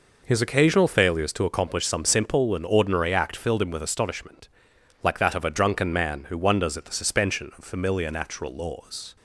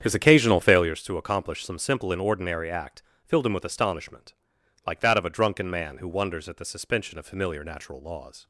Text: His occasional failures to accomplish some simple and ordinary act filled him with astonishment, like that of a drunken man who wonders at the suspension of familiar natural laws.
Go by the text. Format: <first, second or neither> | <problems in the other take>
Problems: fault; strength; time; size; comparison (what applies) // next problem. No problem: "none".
first | starts louder than the rest; strong; until 1.0 s; 8.5 dB // pauses between "act" and "filled"; slight; at 3.0 s; 0.20 s long